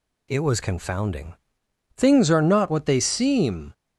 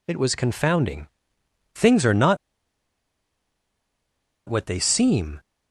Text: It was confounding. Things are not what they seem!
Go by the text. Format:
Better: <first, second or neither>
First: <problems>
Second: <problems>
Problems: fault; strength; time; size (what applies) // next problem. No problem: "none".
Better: first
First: none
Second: pauses between "not" and "what"; strong; at 2.3 s; 2.1 s long